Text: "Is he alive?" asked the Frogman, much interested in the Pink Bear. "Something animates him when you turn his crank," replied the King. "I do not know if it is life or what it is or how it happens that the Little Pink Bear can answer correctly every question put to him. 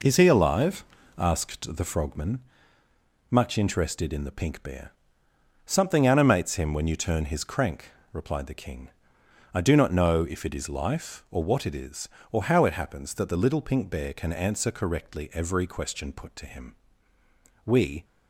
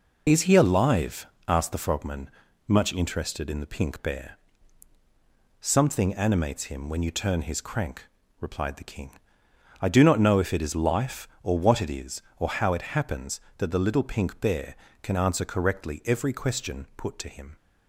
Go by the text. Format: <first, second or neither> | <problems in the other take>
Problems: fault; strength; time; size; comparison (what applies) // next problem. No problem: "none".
second | goes on to say "We"; slight; from 17.6 s on; 0.40 s long